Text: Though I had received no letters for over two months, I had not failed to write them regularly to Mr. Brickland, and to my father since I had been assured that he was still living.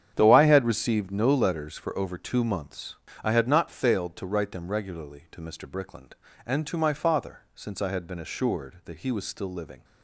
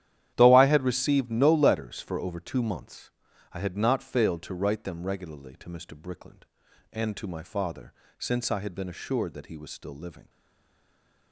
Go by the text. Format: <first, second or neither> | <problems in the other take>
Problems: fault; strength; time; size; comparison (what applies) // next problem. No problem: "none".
first | starts louder than the rest; strong; until 1.3 s; 11 dB; strong in the first // pauses between "father" and "since"; slight; at 7.9 s; 0.24 s long; slight in the first // stays silent after the last word; from 10.2 s on; 1.1 s long